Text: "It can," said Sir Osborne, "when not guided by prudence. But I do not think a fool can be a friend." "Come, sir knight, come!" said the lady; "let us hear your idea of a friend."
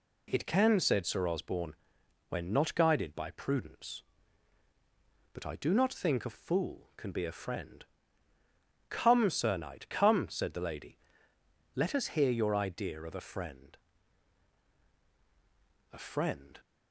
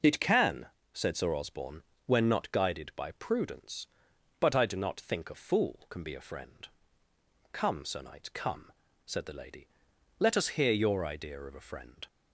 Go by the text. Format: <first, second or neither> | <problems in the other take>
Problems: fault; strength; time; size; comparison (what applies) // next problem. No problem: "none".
second | goes on to say "A friend"; noticeable; from 15.9 s on; 0.66 s long